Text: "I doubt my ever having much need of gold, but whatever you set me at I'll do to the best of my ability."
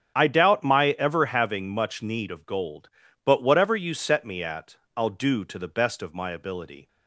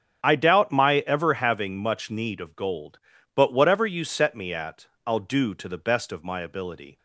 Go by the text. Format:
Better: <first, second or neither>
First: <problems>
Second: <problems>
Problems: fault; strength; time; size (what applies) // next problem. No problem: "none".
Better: neither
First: starts louder than the rest; strong; until 1.1 s; 8 dB // pauses between "at" and "I'll"; slight; at 4.7 s; 0.18 s long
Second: starts louder than the rest; strong; until 1.2 s; 8 dB // pauses between "at" and "I'll"; slight; at 4.8 s; 0.17 s long